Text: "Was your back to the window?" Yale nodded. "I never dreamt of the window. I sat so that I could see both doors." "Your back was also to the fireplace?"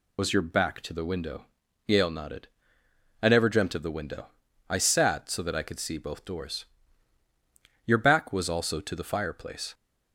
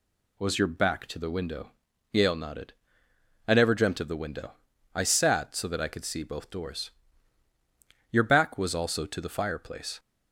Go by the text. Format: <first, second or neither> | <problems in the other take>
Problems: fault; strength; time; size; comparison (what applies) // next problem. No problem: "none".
second | loses the start of "Was"; at 0.1 s; 50 ms